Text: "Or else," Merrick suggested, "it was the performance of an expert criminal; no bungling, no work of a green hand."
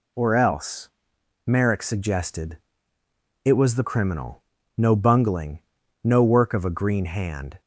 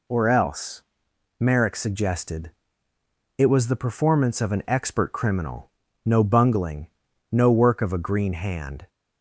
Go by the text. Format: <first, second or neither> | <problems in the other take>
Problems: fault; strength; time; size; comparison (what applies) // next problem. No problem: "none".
second | skips "performance of an expert"; at 3.8 s